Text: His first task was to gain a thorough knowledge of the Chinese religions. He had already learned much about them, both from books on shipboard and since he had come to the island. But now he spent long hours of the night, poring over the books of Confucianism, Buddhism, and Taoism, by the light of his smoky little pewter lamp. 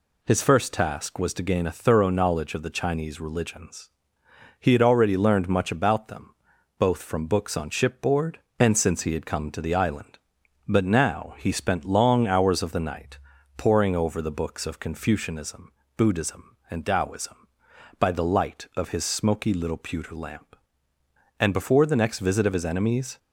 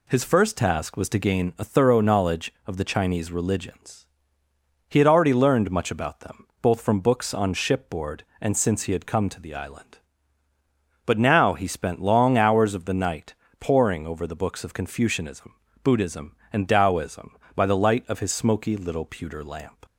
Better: second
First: goes on to say "And before the next visit of his enemies"; strong; from 21.3 s on; 1.7 s long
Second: none

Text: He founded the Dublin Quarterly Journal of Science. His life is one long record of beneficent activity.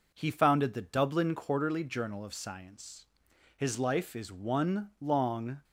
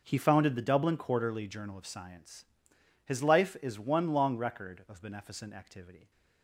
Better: second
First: stops before "record of beneficent activity"; at 5.6 s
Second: none

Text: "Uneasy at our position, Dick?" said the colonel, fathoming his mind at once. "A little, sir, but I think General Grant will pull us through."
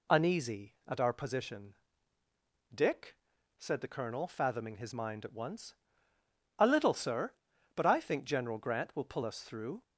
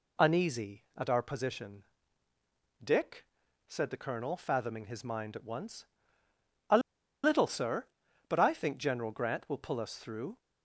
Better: first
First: none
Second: pauses between "A" and "little"; at 6.7 s; 0.44 s long

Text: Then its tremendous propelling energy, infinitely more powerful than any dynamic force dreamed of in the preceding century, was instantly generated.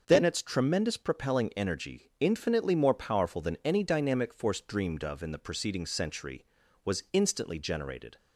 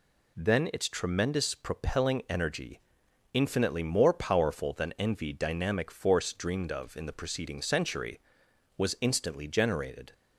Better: first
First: none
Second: says "envy" for "any"; at 4.9 s

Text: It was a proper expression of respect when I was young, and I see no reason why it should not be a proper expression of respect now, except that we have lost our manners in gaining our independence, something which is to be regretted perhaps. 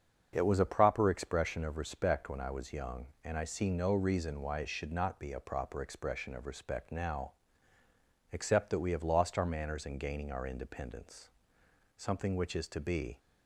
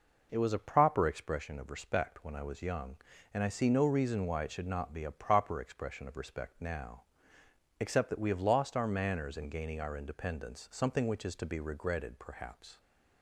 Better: second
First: starts louder than the rest; until 1.3 s; 7 dB // stops before "regretted perhaps"; at 13.1 s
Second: none

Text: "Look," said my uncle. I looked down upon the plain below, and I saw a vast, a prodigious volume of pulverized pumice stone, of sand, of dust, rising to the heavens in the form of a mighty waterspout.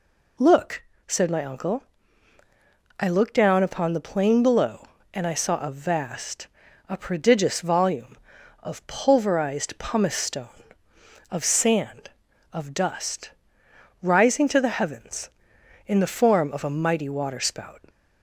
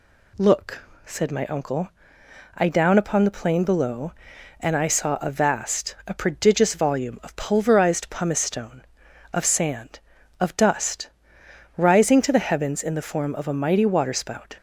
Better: first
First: none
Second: skips "looked"; at 2.6 s

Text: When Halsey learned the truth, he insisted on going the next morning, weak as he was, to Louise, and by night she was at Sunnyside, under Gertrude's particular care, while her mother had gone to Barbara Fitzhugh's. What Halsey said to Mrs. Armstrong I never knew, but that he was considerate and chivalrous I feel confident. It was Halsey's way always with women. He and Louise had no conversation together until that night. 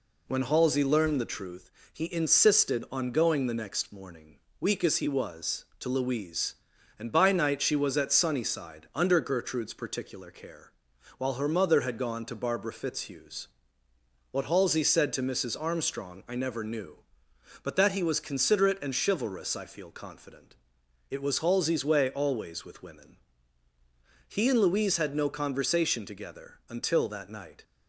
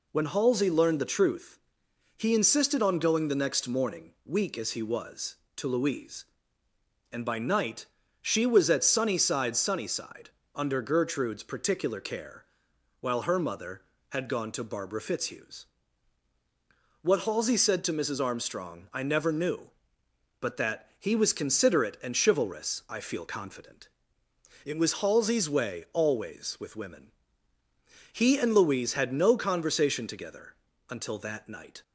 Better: first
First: none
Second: pauses between "night" and "she"; at 7.8 s; 0.38 s long // says "Sunnyside" twice; at 9.5 s // pauses between "together" and "until"; slight; at 30.5 s; 0.34 s long

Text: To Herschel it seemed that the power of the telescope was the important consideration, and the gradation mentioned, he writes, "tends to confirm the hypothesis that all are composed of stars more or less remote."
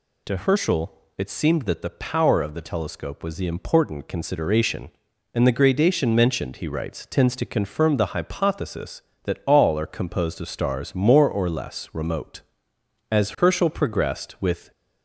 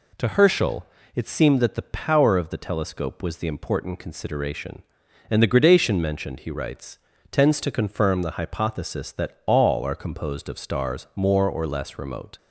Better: second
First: pauses between "Herschel" and "it"; slight; at 0.9 s; 0.24 s long // goes on to say "As Herschel progressed with"; from 13.1 s on; 1.5 s long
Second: pauses between "Herschel" and "it"; slight; at 0.8 s; 0.28 s long

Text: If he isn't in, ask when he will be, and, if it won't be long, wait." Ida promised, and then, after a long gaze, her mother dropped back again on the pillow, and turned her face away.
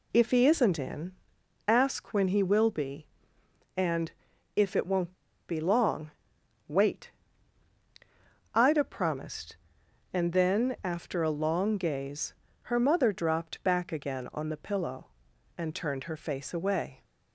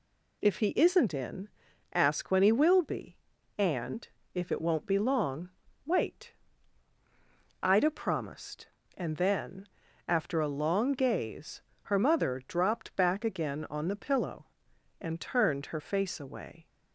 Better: second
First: pauses between "won't" and "be"; at 5.1 s; 0.36 s long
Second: none

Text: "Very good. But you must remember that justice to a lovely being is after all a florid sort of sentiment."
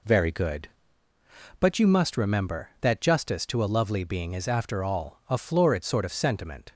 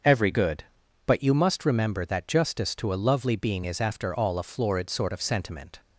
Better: first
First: none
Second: starts louder than the rest; until 1.4 s; 7 dB // says "Every" for "Very"; at 0.0 s

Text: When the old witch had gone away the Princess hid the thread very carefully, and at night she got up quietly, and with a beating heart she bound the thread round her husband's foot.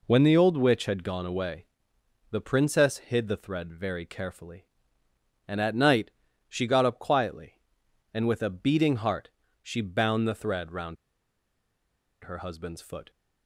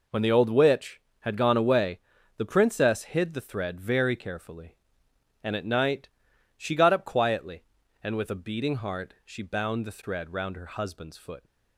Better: second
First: pauses between "away" and "the"; noticeable; at 1.6 s; 0.66 s long // pauses between "night" and "she"; at 6.1 s; 0.38 s long // pauses between "heart" and "she"; slight; at 9.3 s; 0.32 s long // pauses between "round" and "her"; strong; at 10.9 s; 1.2 s long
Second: pauses between "away" and "the"; at 1.9 s; 0.38 s long // pauses between "night" and "she"; noticeable; at 6.0 s; 0.48 s long

